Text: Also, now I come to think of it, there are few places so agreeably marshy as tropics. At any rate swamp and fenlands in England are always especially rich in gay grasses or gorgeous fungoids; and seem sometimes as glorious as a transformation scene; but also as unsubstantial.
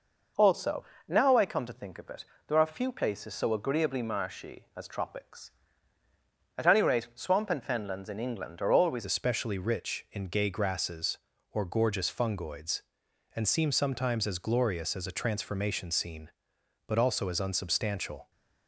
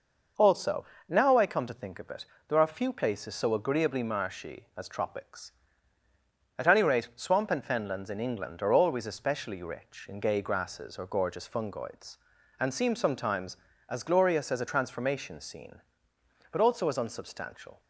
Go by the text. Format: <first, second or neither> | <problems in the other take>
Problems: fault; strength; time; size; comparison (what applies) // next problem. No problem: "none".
second | changes voice at "especially"; from 9.0 s on; 9.3 s long